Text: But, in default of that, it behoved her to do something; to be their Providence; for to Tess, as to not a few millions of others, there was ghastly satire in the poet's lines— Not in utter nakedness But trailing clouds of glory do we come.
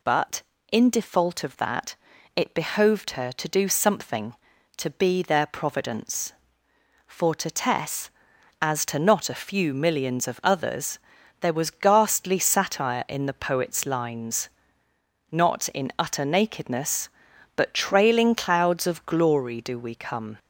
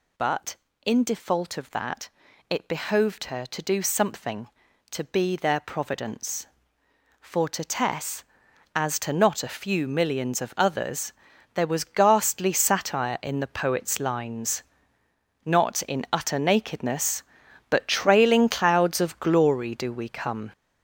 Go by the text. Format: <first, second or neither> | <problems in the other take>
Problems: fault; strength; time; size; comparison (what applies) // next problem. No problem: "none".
first | gets louder; throughout; 6.5 dB